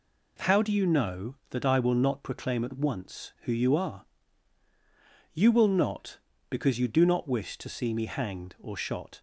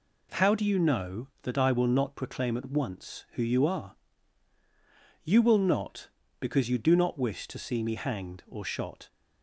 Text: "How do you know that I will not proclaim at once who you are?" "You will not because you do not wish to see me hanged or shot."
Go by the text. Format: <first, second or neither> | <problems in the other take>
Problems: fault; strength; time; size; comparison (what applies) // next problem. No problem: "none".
neither | none